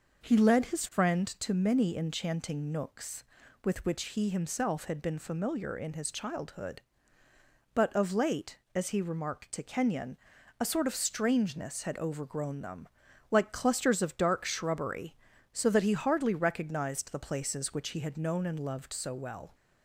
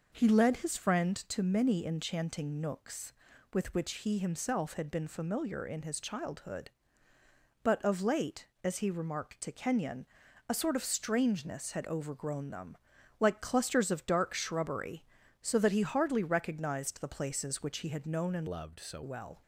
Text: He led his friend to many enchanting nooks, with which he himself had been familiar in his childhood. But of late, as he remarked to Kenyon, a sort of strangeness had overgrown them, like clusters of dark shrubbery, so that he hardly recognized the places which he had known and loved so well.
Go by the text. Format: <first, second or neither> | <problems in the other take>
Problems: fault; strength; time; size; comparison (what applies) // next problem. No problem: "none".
first | changes voice from "loved" to "so"; from 18.4 to 19.0 s; 0.6 s long